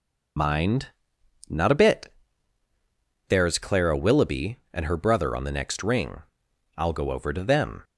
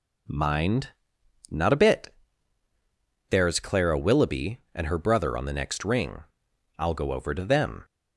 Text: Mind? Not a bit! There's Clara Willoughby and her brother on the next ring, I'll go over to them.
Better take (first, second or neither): second